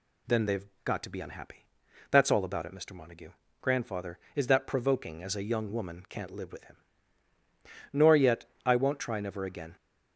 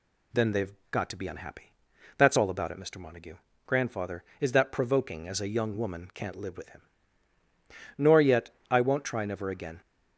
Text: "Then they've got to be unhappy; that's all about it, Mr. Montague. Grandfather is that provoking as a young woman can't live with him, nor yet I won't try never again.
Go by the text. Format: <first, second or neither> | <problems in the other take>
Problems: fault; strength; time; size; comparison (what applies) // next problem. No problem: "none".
neither | pauses between "they've" and "got"; slight; the same in both // pauses between "yet" and "I"; slight; the same in both